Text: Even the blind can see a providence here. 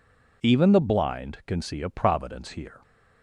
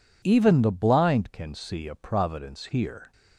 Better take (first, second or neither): neither